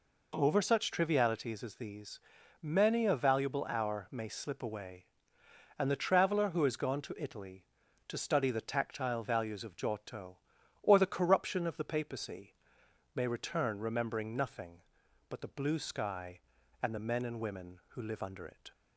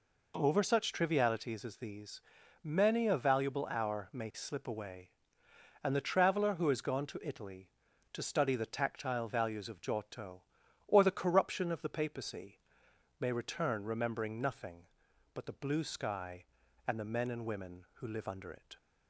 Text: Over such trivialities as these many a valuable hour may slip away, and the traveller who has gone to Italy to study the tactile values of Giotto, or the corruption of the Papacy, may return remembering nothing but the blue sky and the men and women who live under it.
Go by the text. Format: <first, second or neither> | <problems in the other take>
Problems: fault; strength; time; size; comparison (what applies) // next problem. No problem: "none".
neither | pauses between "these" and "many"; the same in both